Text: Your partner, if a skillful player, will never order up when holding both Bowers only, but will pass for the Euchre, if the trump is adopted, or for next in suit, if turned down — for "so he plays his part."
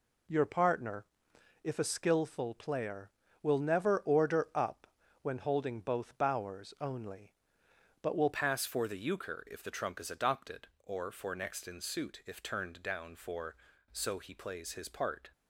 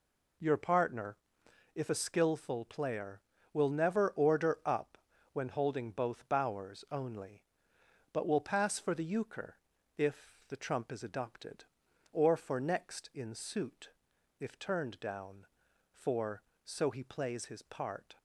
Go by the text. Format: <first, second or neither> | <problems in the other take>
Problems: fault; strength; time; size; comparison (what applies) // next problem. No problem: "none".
second | pauses between "up" and "when"; slight; at 4.8 s; 0.34 s long; slight in the second // changes voice at "pass"; from 8.3 s on; 7.0 s long